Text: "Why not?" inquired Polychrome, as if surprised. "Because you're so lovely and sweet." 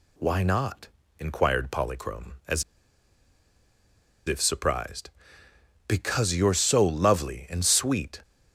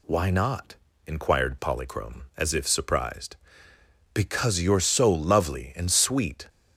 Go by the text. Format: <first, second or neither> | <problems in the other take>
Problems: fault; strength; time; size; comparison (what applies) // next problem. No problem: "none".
second | pauses between "as" and "if"; strong; at 2.6 s; 1.6 s long